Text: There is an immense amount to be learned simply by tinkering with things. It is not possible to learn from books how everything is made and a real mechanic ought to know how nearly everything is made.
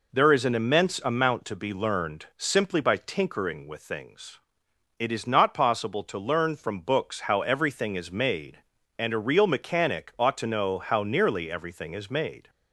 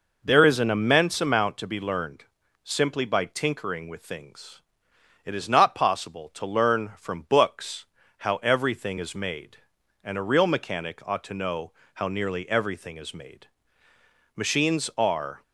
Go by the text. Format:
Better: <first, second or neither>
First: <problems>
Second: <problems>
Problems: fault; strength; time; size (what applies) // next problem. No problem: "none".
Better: first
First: none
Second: pauses between "learned" and "simply"; at 2.2 s; 0.40 s long // pauses between "books" and "how"; slight; at 7.8 s; 0.32 s long // pauses between "know" and "how"; slight; at 11.7 s; 0.22 s long // goes on to say "Machines are"; noticeable; from 14.3 s on; 1.0 s long